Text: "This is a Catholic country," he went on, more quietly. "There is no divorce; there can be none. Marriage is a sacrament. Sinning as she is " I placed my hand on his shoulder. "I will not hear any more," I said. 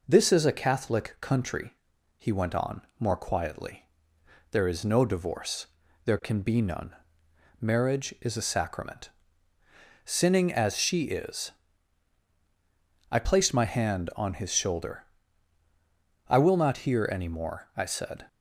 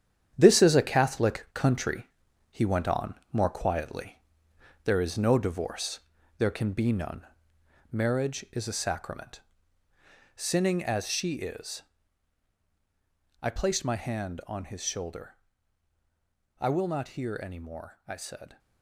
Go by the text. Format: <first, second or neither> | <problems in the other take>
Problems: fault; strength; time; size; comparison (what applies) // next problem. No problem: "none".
first | gets quieter; strong; throughout; 13.5 dB